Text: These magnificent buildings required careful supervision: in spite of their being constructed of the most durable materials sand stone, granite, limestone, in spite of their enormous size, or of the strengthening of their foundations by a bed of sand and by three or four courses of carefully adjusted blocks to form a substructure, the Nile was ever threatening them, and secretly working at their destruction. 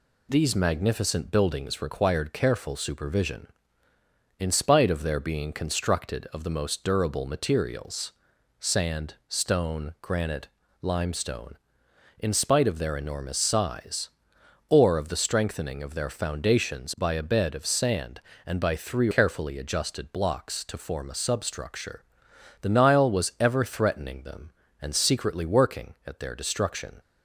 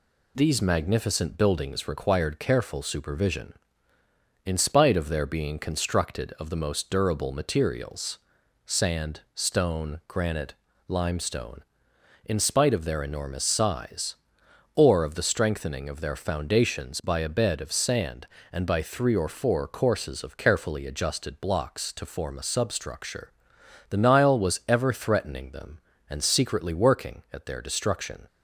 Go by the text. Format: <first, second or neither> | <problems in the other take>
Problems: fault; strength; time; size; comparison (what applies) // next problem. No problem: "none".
second | pauses between "materials" and "sand"; noticeable; at 8.1 s; 0.48 s long; noticeable in the second // skips "or four courses of"; at 19.1 s